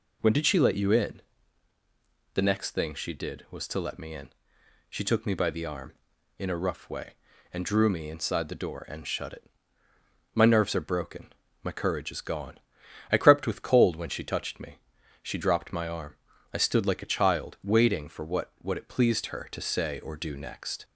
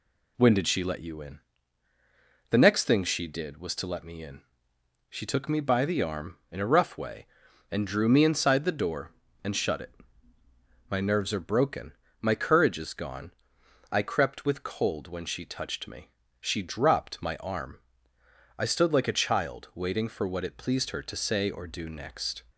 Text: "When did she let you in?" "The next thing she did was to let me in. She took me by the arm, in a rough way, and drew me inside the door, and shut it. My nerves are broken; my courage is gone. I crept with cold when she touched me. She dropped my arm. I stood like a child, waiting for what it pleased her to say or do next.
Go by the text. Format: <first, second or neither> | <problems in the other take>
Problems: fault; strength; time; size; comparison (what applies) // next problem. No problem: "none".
second | says "what" twice; at 18.5 s